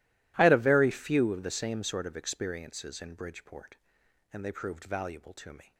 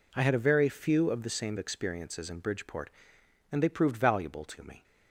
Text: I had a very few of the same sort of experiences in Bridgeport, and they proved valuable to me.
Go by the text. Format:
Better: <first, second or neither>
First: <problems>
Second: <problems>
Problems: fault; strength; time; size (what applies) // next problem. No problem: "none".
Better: first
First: none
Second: skips "sort of"; at 1.5 s